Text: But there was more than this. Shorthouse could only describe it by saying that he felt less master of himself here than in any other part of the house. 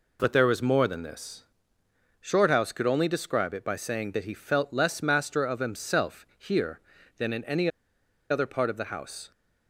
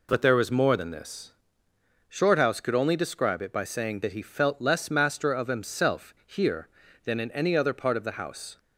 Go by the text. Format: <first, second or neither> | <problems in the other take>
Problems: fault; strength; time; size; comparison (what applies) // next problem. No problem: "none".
second | pauses between "any" and "other"; noticeable; at 7.7 s; 0.60 s long